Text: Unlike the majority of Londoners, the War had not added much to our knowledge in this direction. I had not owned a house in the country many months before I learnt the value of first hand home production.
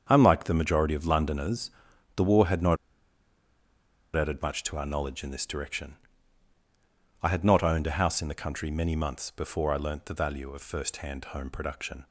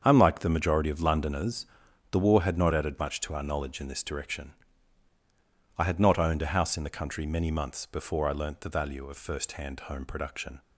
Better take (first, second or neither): second